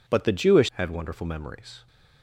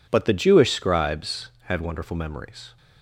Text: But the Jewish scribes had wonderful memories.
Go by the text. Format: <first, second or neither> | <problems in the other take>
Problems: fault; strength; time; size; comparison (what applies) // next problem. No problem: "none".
second | skips "scribes"; at 0.7 s